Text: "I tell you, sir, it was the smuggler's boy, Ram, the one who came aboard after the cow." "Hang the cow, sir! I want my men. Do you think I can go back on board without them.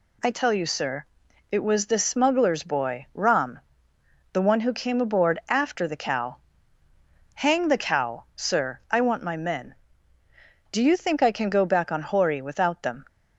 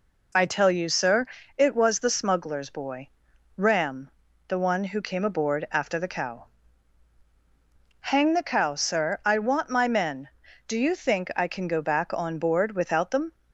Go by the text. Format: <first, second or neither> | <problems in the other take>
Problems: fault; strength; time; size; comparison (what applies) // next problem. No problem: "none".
second | says "hori" for "board"; at 12.0 s